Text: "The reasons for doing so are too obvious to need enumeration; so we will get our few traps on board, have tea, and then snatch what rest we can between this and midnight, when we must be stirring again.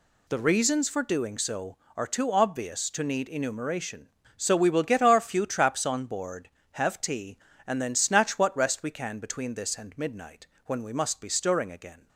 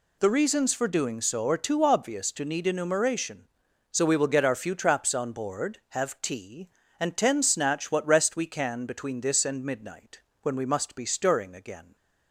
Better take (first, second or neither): first